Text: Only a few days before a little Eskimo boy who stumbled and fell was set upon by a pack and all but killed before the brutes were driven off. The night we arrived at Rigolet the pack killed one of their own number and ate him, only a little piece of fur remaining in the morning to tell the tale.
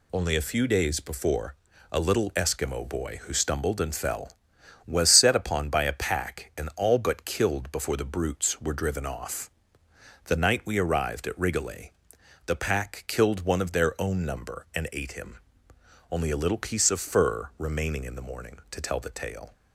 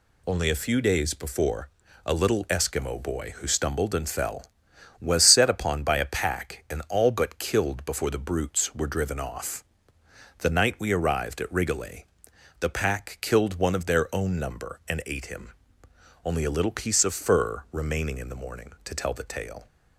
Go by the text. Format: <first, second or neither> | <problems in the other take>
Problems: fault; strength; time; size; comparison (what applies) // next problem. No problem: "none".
neither | pauses between "before" and "a"; the same in both // pauses between "Rigolet" and "the"; noticeable; the same in both